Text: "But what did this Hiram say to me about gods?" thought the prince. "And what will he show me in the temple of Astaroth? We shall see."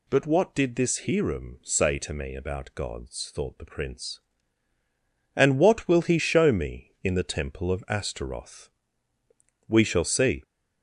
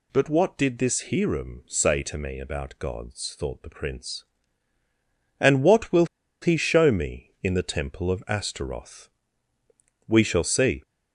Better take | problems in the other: first | pauses between "will" and "he"; slight; at 6.0 s; 0.35 s long

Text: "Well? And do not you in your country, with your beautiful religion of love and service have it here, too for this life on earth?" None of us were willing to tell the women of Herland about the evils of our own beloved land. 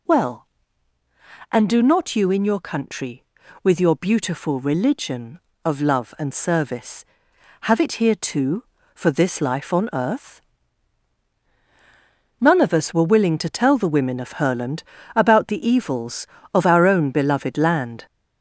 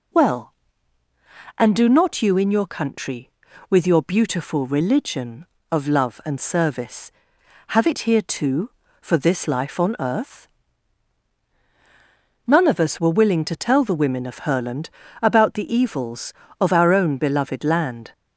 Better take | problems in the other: second | gets louder; noticeable; throughout; 4.5 dB // pauses between "Herland" and "about"; slight; at 14.8 s; 0.32 s long; slight in the second

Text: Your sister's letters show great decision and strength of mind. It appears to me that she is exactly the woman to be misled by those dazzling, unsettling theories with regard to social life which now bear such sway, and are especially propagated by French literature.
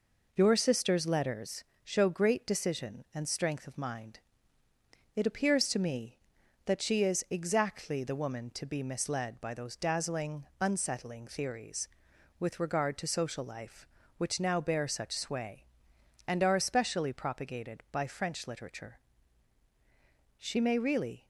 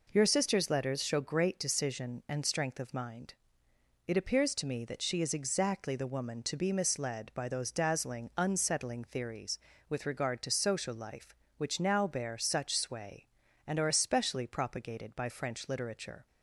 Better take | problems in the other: second | pauses between "letters" and "show"; slight; at 1.6 s; 0.18 s long // goes on to say "She may really"; noticeable; from 20.3 s on; 0.88 s long

